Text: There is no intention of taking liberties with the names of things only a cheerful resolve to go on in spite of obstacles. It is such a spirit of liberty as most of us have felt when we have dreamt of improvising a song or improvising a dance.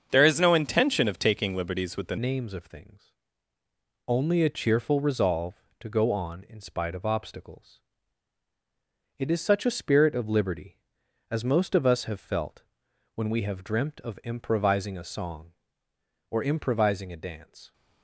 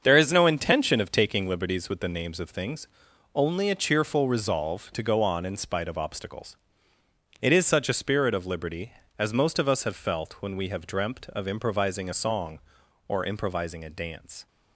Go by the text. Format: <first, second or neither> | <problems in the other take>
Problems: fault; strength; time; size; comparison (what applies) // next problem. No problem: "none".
second | starts louder than the rest; strong; until 1.1 s; 7 dB; also in the second // changes voice at "names"; from 2.1 s on; 15.6 s long // pauses between "things" and "only"; noticeable; at 3.1 s; 0.96 s long; noticeable in the second // pauses between "felt" and "when"; noticeable; at 12.6 s; 0.52 s long